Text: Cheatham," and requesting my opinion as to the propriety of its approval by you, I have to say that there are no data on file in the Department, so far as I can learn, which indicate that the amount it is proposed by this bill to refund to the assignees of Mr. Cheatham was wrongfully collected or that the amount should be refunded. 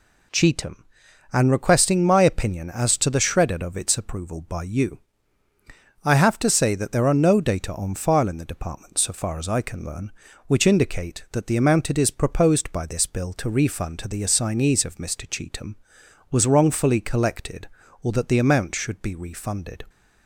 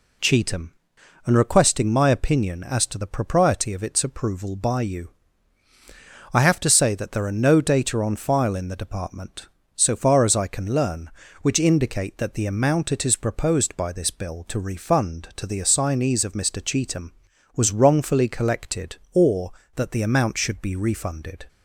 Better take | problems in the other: second | says "shredded" for "propriety"; at 3.1 s

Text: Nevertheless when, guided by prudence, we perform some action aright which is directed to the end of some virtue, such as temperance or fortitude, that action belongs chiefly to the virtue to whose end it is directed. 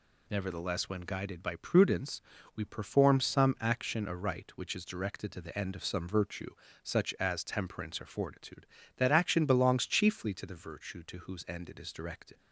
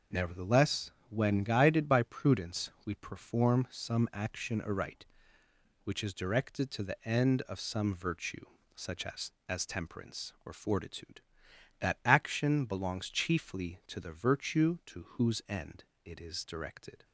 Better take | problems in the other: first | pauses between "Nevertheless" and "when"; slight; at 0.9 s; 0.16 s long // says "as" twice; at 9.4 s // pauses between "end" and "it"; slight; at 15.8 s; 0.20 s long

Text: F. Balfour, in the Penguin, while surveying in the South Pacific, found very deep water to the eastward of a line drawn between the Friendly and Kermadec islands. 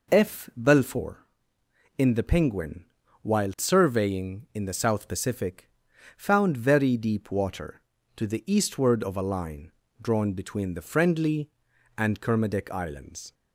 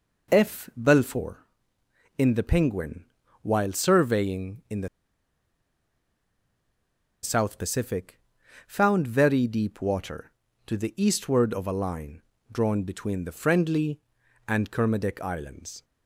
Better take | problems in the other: first | pauses between "the" and "South"; strong; at 4.8 s; 2.3 s long // pauses between "line" and "drawn"; slight; at 12.2 s; 0.28 s long; slight in the first

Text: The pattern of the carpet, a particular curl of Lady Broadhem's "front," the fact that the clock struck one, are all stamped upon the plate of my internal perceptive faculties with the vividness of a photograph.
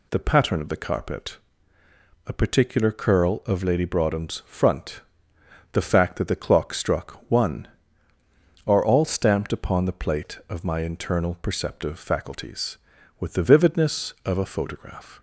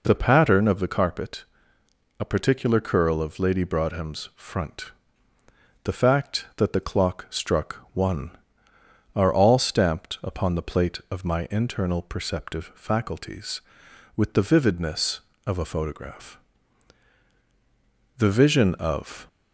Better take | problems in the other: first | goes on to say "The vision of"; noticeable; from 18.1 s on; 1.0 s long

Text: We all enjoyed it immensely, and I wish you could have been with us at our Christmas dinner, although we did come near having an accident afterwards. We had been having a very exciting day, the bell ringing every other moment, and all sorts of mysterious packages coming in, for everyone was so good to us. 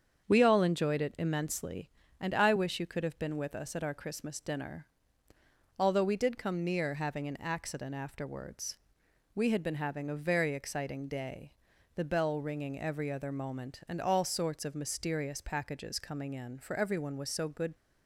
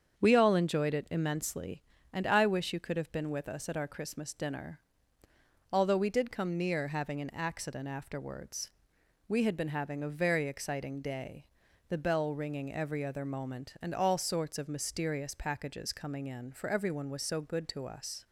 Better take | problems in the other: second | starts louder than the rest; strong; until 1.3 s; 7.5 dB; strong in the second // stops before "to us"; at 17.7 s

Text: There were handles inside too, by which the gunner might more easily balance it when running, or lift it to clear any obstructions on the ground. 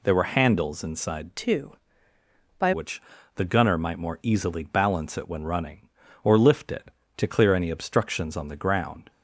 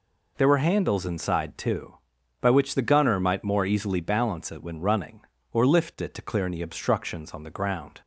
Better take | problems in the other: second | changes voice from "too" to "by"; from 1.3 to 2.7 s; 1.4 s long // pauses between "which" and "the"; slight; at 2.9 s; 0.36 s long

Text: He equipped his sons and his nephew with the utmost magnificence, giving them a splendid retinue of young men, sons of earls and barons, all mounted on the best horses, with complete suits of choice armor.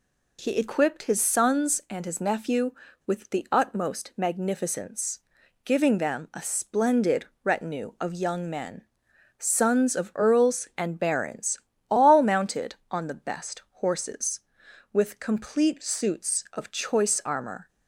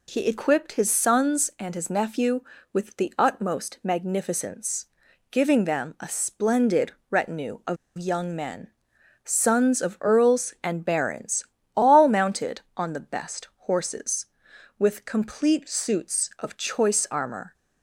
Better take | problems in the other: first | pauses between "splendid" and "retinue"; slight; at 6.9 s; 0.18 s long; slight in the first // pauses between "of" and "young"; slight; at 7.7 s; 0.21 s long

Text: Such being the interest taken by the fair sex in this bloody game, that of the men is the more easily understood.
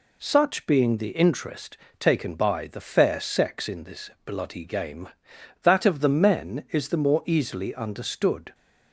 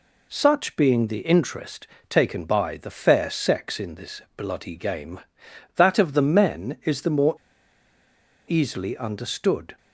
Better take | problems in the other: first | pauses between "interest" and "taken"; slight; at 1.8 s; 0.20 s long; slight in the first // pauses between "this" and "bloody"; slight; at 4.2 s; 0.16 s long; slight in the first // pauses between "more" and "easily"; at 7.3 s; 1.1 s long

